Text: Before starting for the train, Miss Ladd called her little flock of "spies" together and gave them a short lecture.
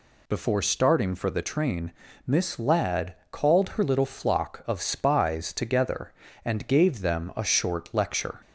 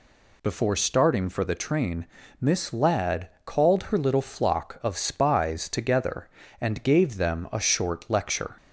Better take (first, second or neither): neither